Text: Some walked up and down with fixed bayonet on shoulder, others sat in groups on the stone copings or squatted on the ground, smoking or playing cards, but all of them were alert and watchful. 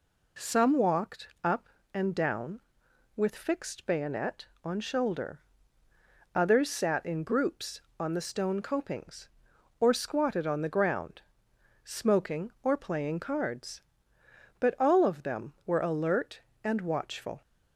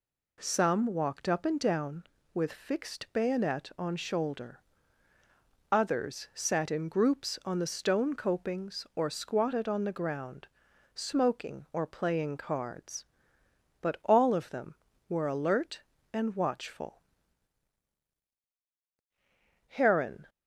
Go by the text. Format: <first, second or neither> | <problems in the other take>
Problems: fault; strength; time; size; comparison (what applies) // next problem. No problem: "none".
first | goes on to say "Heron"; noticeable; from 19.6 s on; 0.62 s long